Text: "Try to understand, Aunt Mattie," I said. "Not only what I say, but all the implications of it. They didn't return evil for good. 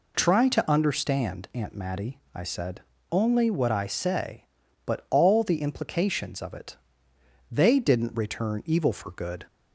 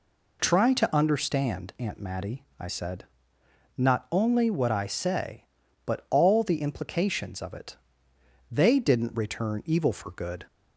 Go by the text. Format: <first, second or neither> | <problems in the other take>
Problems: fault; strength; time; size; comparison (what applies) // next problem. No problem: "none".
second | skips "Not"; at 2.9 s